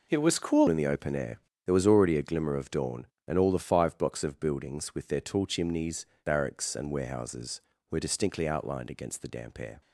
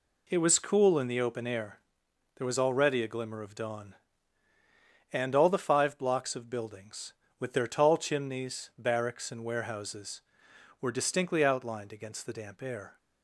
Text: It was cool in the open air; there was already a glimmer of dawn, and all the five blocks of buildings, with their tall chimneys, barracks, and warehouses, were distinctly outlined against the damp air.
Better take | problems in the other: second | changes voice at "in"; from 0.6 s on; 9.2 s long

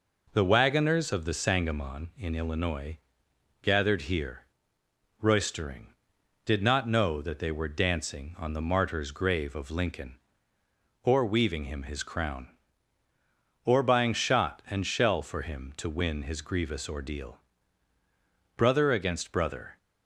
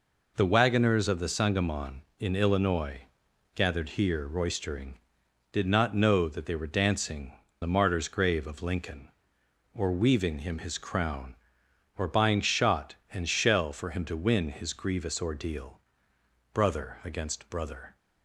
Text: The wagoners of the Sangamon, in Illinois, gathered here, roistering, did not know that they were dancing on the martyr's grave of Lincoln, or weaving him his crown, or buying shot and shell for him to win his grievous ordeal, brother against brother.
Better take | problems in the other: first | skips "on"; at 7.4 s

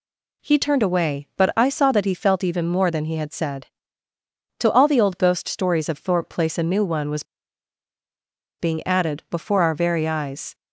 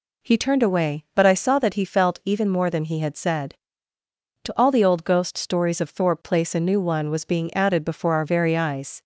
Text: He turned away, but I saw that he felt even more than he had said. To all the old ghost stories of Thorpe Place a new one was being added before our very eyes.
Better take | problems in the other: second | pauses between "was" and "being"; strong; at 7.2 s; 1.3 s long

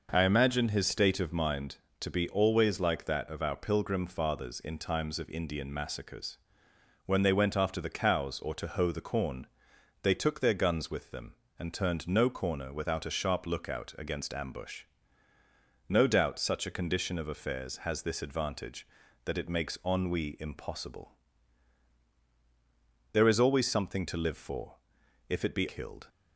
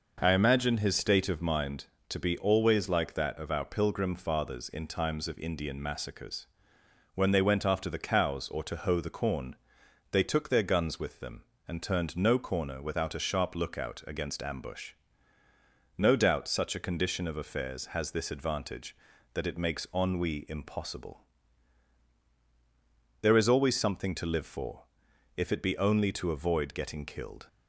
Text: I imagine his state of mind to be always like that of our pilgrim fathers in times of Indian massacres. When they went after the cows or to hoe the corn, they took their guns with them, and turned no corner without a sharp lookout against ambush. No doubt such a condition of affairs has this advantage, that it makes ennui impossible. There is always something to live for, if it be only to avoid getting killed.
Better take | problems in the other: second | skips "only to avoid getting"; at 25.6 s

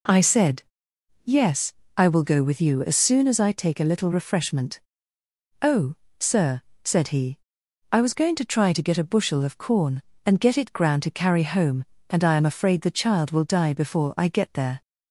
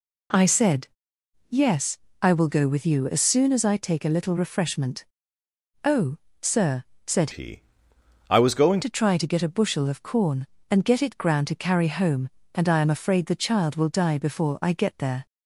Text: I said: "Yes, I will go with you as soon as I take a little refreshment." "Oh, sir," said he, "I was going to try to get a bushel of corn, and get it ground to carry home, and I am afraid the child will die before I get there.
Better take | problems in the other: first | changes voice from "he" to "going"; from 7.3 to 8.8 s; 1.5 s long

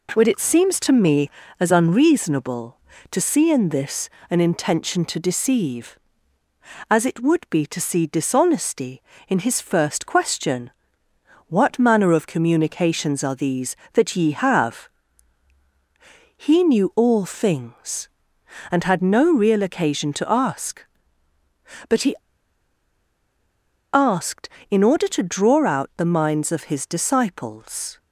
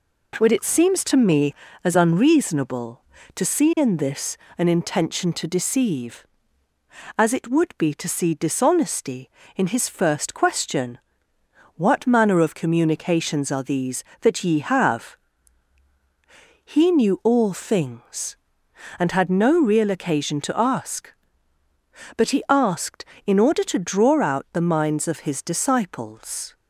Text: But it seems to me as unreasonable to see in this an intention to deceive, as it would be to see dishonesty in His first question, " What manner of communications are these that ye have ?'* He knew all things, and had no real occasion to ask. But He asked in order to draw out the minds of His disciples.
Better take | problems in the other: second | pauses between "this" and "an"; slight; at 4.0 s; 0.20 s long; slight in the second // pauses between "He" and "asked"; strong; at 22.1 s; 1.7 s long

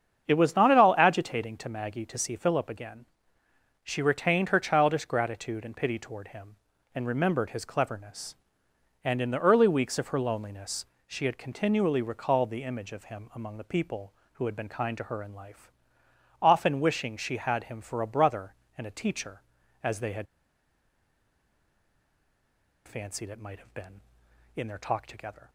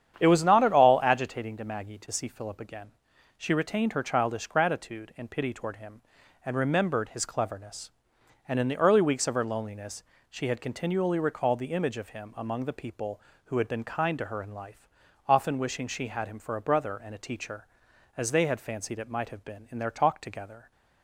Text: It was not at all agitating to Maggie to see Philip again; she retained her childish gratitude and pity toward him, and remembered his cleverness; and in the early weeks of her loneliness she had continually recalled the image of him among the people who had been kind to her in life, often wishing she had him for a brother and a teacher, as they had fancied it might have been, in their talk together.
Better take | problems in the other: second | starts louder than the rest; strong; until 1.2 s; 7.5 dB; strong in the second // pauses between "loneliness" and "she"; slight; at 10.8 s; 0.22 s long; slight in the second // pauses between "had" and "fancied"; strong; at 20.2 s; 2.6 s long

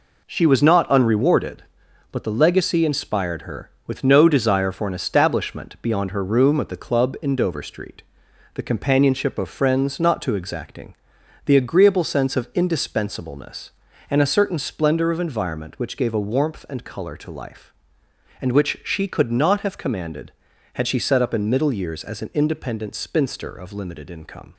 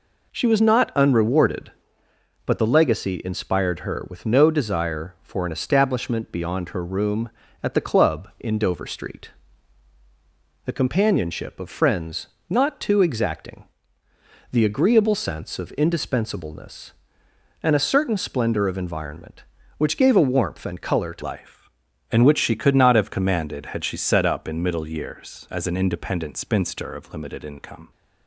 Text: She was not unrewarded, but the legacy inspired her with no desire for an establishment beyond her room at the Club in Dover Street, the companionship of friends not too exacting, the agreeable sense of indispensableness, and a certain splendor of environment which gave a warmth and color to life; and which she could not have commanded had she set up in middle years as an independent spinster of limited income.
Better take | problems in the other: first | pauses between "friends" and "not"; slight; at 12.2 s; 0.20 s long // changes voice at "life"; from 21.2 s on; 6.7 s long

